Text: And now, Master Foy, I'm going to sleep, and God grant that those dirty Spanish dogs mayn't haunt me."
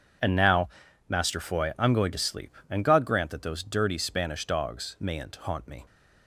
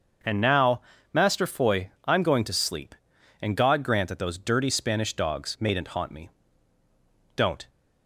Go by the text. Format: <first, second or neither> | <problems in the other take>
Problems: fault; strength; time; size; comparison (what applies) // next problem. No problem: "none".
first | starts louder than the rest; until 1.5 s; 6.5 dB // goes on to say "Don't"; slight; from 7.3 s on; 0.32 s long